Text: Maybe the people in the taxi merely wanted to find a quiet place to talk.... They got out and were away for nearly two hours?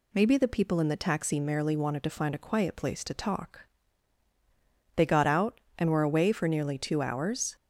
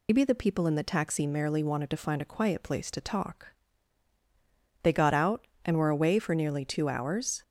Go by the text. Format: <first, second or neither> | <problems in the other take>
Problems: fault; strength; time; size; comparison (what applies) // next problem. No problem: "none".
first | loses the start of "Maybe"; at 0.0 s; 90 ms